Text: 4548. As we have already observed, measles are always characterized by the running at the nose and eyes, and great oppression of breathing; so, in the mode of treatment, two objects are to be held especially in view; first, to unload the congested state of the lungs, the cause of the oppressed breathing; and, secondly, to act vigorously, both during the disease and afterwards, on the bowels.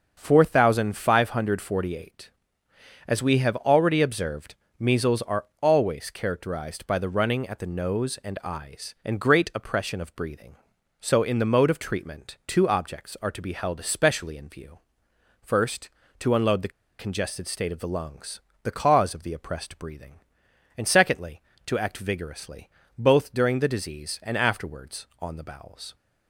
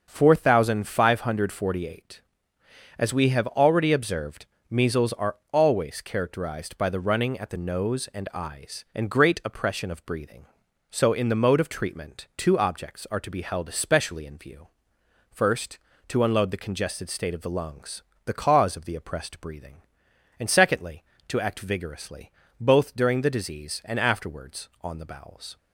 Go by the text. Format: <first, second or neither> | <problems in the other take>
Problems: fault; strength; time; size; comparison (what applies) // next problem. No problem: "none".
second | starts louder than the rest; until 1.1 s; 6.5 dB; also in the second // pauses between "are" and "always"; slight; at 5.4 s; 0.18 s long; slight in the second // pauses between "the" and "congested"; slight; at 16.7 s; 0.28 s long